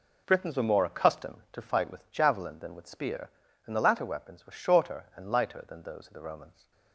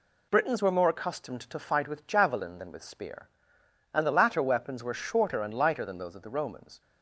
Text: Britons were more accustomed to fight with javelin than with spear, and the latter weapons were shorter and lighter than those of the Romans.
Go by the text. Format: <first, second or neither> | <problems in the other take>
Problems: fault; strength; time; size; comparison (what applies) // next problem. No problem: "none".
neither | none